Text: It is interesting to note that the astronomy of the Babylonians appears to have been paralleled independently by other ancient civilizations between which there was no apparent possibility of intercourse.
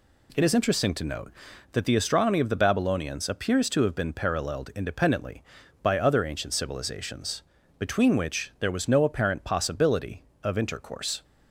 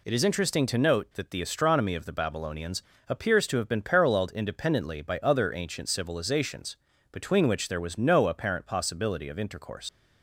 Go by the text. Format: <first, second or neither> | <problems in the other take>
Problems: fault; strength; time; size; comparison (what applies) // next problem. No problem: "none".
first | pauses between "Babylonians" and "appears"; slight; at 2.8 s; 0.26 s long // pauses between "civilizations" and "between"; slight; at 6.7 s; 0.36 s long; also in the first // leaves "intercourse" unfinished; at 9.8 s; 85 ms